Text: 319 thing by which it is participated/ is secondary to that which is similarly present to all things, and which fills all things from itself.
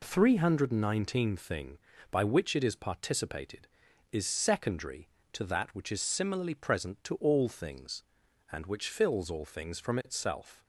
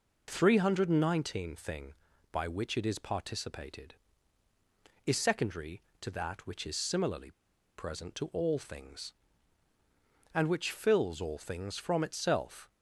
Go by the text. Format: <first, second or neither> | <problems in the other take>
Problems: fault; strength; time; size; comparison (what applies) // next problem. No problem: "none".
first | pauses between "similarly" and "present"; noticeable; at 7.2 s; 0.46 s long